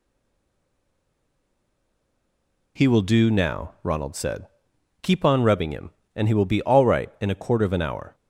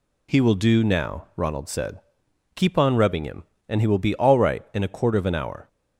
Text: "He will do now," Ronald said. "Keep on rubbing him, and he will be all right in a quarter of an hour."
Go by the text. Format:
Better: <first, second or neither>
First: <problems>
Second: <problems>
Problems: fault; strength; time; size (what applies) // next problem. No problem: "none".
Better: second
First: stays silent before the first word; strong; until 2.7 s; 2.7 s long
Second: none